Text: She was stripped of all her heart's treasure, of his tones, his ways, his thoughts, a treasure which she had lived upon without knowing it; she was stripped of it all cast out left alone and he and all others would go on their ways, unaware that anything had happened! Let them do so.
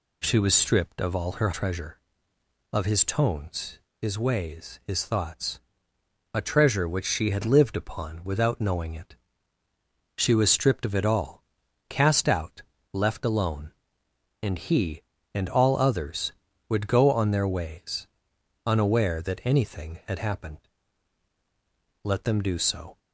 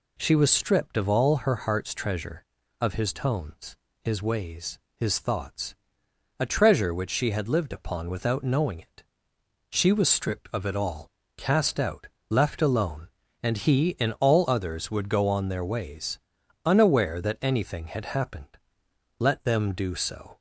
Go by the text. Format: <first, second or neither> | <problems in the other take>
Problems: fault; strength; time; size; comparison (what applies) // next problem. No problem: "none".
second | skips "heart's"; at 1.5 s // pauses between "all" and "cast"; noticeable; at 11.4 s; 0.46 s long; slight in the second // pauses between "out" and "left"; slight; at 12.6 s; 0.32 s long; slight in the second